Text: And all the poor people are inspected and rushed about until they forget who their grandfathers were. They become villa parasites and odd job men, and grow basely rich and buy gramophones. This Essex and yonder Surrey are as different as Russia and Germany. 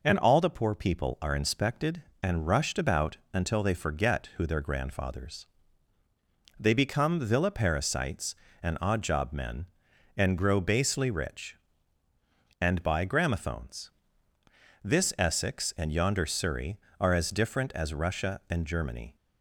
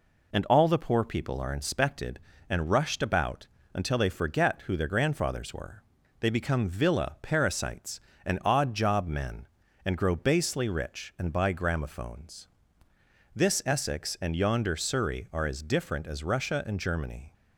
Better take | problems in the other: second | pauses between "about" and "until"; slight; at 3.1 s; 0.16 s long; slight in the second // skips "were"; at 6.0 s

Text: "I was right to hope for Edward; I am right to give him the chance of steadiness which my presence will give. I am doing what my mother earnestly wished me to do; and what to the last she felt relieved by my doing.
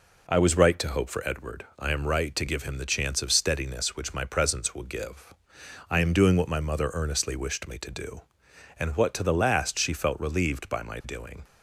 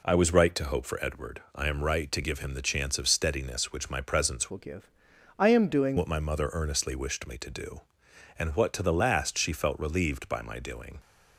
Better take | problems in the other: first | changes voice from "will" to "doing"; from 4.4 to 5.9 s; 1.5 s long

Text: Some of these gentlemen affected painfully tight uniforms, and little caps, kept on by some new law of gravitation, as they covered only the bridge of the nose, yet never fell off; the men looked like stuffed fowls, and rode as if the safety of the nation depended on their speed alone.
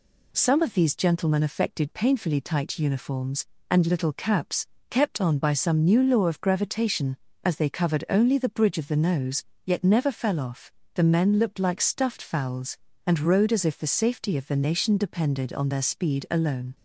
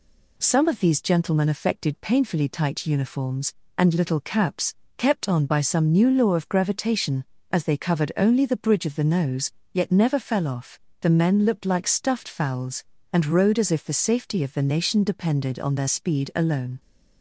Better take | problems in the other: neither | none

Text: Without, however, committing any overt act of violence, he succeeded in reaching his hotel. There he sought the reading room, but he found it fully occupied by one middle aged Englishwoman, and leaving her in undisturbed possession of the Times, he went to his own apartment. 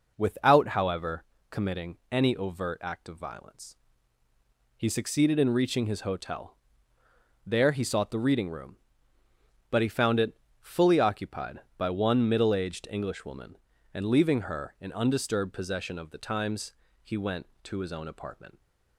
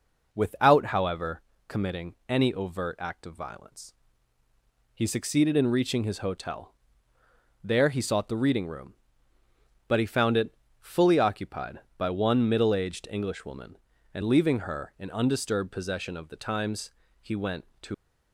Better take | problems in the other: first | pauses between "it" and "fully"; slight; at 10.5 s; 0.24 s long; slight in the first // stops before "his own apartment"; at 17.9 s

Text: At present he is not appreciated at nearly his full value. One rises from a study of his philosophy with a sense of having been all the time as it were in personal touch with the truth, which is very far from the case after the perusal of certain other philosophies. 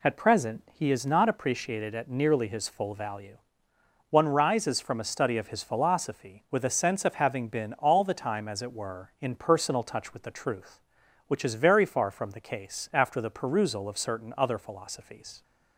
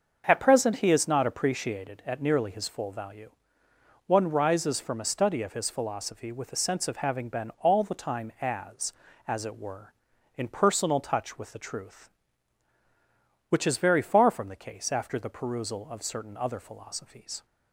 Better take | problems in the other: first | starts louder than the rest; until 1.2 s; 6.5 dB // says "as" twice; at 9.2 s

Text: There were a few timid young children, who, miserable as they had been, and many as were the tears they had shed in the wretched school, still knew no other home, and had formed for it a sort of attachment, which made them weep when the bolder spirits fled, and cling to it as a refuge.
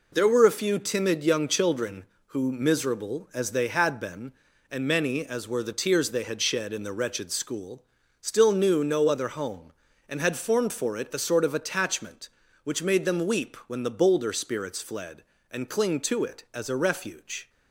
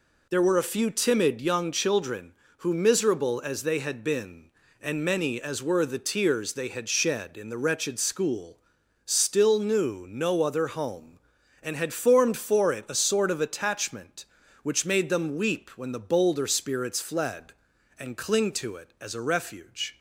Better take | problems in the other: neither | none

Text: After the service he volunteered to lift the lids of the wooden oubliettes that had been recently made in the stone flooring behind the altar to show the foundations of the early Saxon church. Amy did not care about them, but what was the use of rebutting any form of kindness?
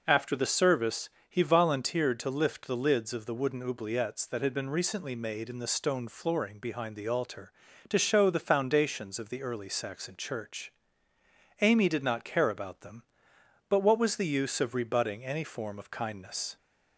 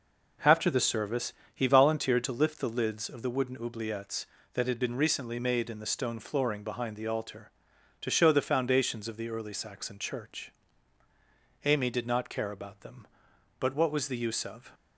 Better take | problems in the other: first | pauses between "service" and "he"; slight; at 1.3 s; 0.20 s long; slight in the first // stops before "rebutting any form of kindness"; at 14.7 s

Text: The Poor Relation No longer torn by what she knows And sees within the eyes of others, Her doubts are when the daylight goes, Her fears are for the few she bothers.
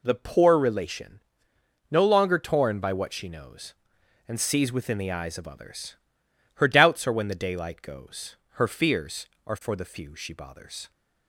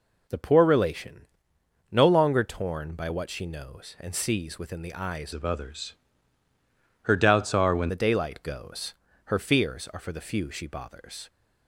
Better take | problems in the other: first | pauses between "Relation" and "No"; noticeable; at 1.2 s; 0.66 s long; noticeable in the first // changes voice from "of" to "when"; from 5.3 to 7.8 s; 2.5 s long

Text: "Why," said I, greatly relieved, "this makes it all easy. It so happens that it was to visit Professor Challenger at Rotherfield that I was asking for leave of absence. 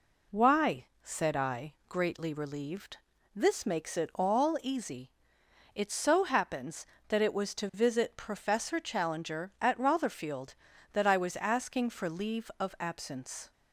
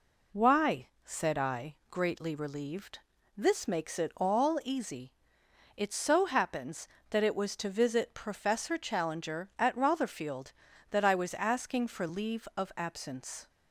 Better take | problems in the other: neither | none

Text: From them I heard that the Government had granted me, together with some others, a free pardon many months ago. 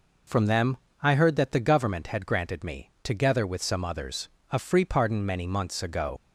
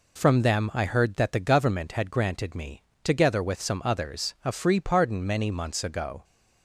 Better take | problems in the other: second | pauses between "them" and "I"; slight; at 0.7 s; 0.26 s long // leaves "ago" unfinished; at 6.1 s; 95 ms

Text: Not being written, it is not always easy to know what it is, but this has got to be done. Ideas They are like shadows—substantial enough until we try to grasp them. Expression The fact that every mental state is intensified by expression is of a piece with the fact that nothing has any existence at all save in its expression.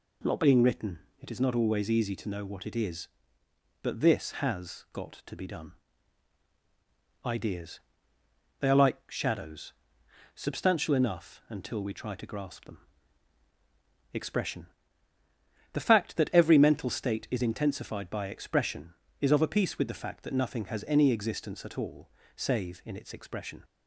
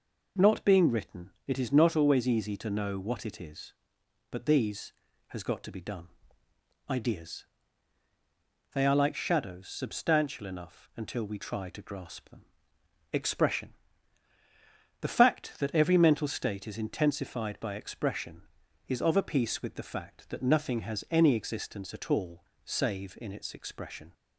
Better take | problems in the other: first | says "these" for "this"; at 4.4 s // pauses between "Ideas" and "They"; strong; at 7.4 s; 1.3 s long; noticeable in the first // pauses between "Expression" and "The"; strong; at 13.7 s; 1.2 s long; also in the first // pauses between "all" and "save"; slight; at 22.4 s; 0.20 s long; slight in the first

